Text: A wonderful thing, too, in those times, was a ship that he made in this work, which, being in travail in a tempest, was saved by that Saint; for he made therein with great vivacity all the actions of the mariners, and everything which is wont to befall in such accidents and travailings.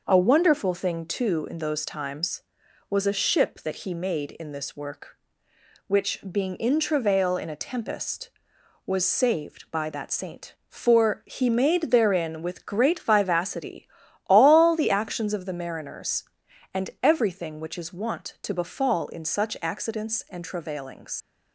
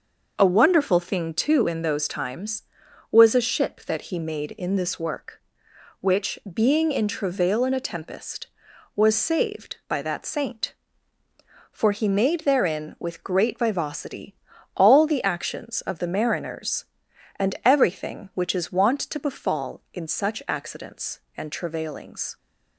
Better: second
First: pauses between "vivacity" and "all"; at 13.8 s; 0.38 s long // leaves "travailings" unfinished; at 21.2 s; 90 ms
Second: pauses between "vivacity" and "all"; at 14.3 s; 0.40 s long

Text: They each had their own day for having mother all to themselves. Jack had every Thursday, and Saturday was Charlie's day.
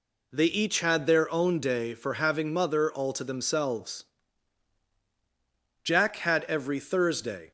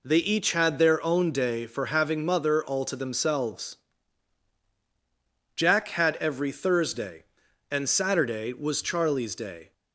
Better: second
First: stops before "and Saturday was Charlie's day"; at 7.4 s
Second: none

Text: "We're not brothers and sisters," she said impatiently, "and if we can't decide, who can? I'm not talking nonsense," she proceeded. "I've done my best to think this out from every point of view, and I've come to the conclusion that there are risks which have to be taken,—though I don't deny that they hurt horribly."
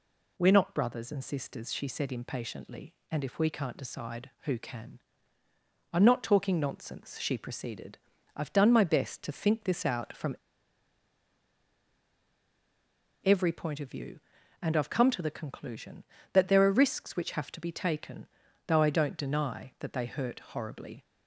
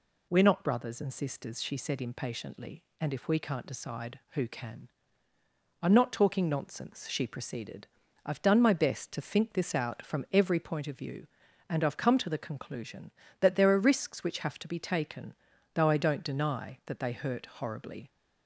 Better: second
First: pauses between "from" and "every"; strong; at 10.3 s; 2.8 s long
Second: none

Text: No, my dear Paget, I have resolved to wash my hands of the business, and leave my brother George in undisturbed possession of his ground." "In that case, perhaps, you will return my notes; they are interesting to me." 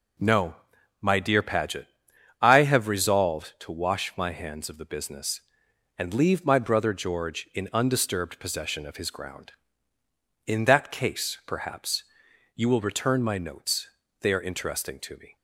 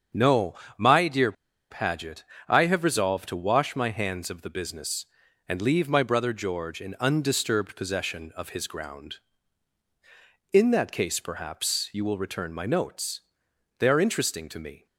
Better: first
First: none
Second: starts louder than the rest; strong; until 1.7 s; 7 dB // pauses between "dear" and "Paget"; at 1.3 s; 0.38 s long

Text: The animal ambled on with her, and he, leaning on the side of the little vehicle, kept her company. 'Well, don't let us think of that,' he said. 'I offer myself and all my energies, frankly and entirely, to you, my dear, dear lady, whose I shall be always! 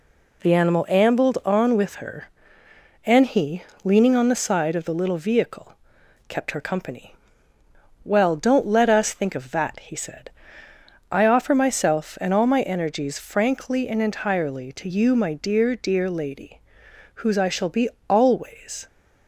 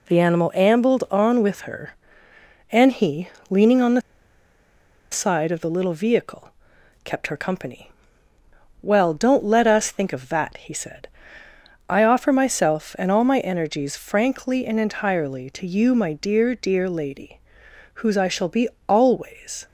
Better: first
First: pauses between "be" and "always"; slight; at 17.8 s; 0.18 s long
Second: pauses between "the" and "side"; at 4.0 s; 1.1 s long // pauses between "be" and "always"; slight; at 18.6 s; 0.18 s long

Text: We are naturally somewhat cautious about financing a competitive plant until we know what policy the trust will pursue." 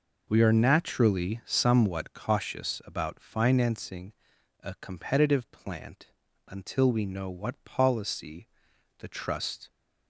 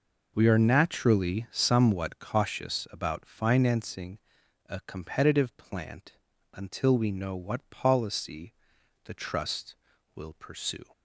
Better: second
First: pauses between "financing" and "a"; noticeable; at 4.1 s; 0.50 s long // pauses between "plant" and "until"; at 6.0 s; 0.42 s long // pauses between "policy" and "the"; noticeable; at 8.4 s; 0.52 s long // stops before "will pursue"; at 9.7 s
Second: pauses between "financing" and "a"; noticeable; at 4.1 s; 0.50 s long // pauses between "plant" and "until"; at 6.1 s; 0.42 s long // pauses between "policy" and "the"; noticeable; at 8.5 s; 0.52 s long

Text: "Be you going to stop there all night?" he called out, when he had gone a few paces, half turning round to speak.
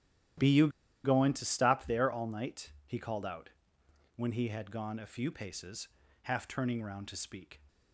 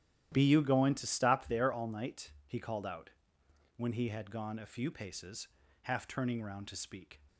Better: second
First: starts louder than the rest; strong; until 1.7 s; 12 dB // pauses between "you" and "going"; slight; at 0.6 s; 0.35 s long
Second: starts louder than the rest; strong; until 1.3 s; 11.5 dB

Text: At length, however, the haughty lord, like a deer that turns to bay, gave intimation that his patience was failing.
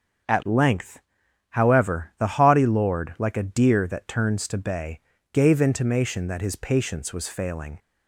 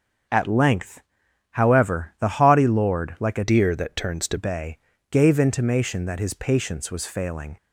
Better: first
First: starts louder than the rest; strong; until 1.8 s; 7 dB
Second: starts louder than the rest; until 1.8 s; 7 dB // changes voice from "deer" to "to"; from 3.4 to 4.3 s; 0.9 s long

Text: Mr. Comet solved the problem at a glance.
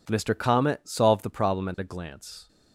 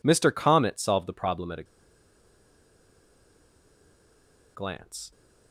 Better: first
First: none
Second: pauses between "a" and "glance"; strong; at 1.6 s; 2.9 s long

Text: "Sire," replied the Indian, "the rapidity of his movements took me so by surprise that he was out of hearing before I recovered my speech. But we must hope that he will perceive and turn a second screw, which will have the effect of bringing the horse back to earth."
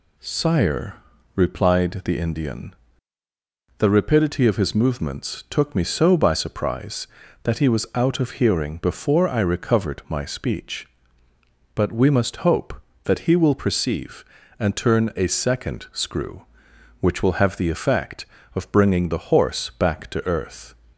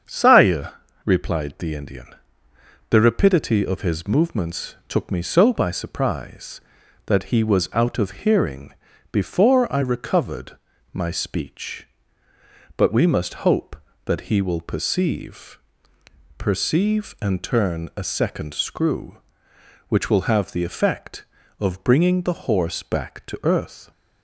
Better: first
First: none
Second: starts louder than the rest; strong; until 1.3 s; 7 dB // pauses between "hearing" and "before"; at 8.7 s; 0.38 s long // pauses between "recovered" and "my"; slight; at 10.5 s; 0.34 s long // says "perceive" twice; at 16.3 s

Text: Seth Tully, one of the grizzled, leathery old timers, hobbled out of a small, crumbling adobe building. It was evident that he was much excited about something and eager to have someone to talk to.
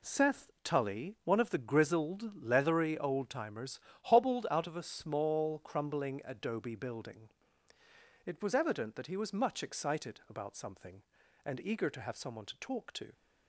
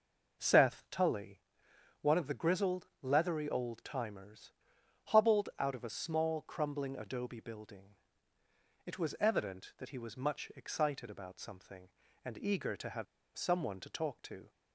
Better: first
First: none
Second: pauses between "have" and "someone"; slight; at 13.0 s; 0.32 s long

